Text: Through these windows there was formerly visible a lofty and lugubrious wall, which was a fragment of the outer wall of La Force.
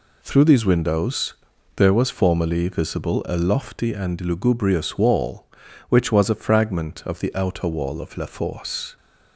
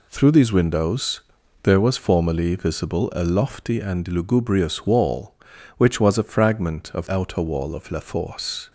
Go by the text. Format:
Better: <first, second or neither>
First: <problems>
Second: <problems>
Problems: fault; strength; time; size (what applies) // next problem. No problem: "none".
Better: first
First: pauses between "windows" and "there"; at 1.3 s; 0.42 s long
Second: pauses between "windows" and "there"; at 1.2 s; 0.42 s long // skips "the"; at 7.0 s